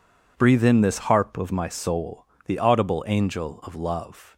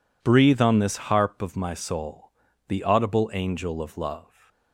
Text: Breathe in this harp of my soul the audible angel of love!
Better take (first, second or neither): first